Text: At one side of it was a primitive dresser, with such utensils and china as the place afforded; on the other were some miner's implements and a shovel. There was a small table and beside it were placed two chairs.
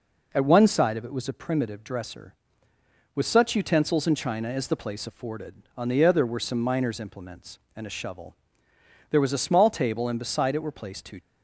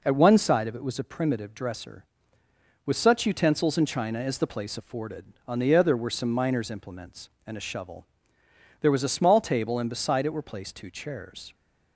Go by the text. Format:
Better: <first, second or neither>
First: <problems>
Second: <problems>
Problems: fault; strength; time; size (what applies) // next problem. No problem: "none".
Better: second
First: stops before "chairs"; at 11.1 s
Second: none